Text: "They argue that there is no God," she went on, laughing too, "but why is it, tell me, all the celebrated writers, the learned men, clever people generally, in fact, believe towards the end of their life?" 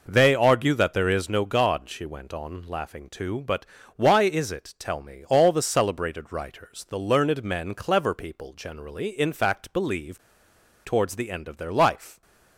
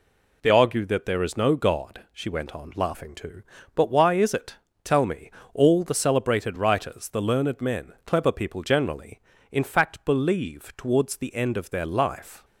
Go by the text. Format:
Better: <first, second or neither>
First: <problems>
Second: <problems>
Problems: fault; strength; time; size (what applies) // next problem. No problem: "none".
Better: second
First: pauses between "but" and "why"; slight; at 3.6 s; 0.32 s long // pauses between "believe" and "towards"; noticeable; at 10.2 s; 0.64 s long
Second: none